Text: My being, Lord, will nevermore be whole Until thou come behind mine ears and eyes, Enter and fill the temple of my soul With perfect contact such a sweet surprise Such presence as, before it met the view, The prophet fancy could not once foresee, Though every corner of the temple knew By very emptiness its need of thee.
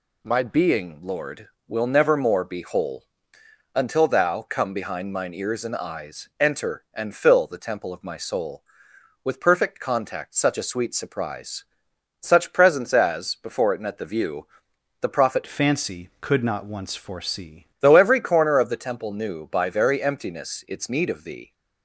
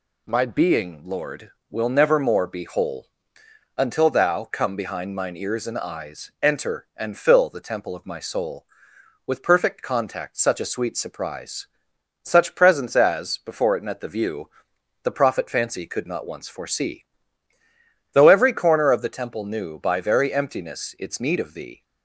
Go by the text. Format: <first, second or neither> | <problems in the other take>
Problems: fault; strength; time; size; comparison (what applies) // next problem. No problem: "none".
second | pauses between "whole" and "Until"; noticeable; at 3.0 s; 0.66 s long; noticeable in the second // pauses between "surprise" and "Such"; noticeable; at 11.6 s; 0.56 s long; noticeable in the second // changes voice from "fancy" to "foresee"; from 15.4 to 17.6 s; 2.2 s long